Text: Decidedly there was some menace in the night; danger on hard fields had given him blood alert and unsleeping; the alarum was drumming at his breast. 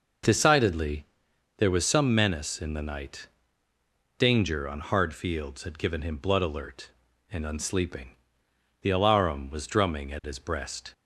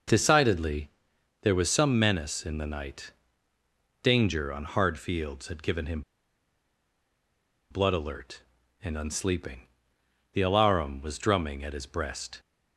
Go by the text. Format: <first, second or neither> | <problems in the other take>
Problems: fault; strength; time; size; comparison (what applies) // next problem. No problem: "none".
first | pauses between "Decidedly" and "there"; noticeable; at 0.8 s; 0.54 s long; noticeable in the first // pauses between "him" and "blood"; strong; at 6.0 s; 1.7 s long